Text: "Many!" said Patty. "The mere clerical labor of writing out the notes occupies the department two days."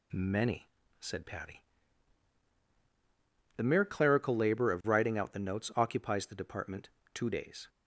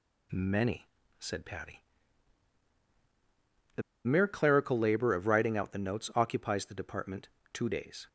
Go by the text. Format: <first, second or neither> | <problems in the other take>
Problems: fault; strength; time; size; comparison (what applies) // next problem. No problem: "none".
first | pauses between "The" and "mere"; slight; at 3.8 s; 0.23 s long // pauses between "department" and "two"; slight; at 7.2 s; 0.26 s long; slight in the first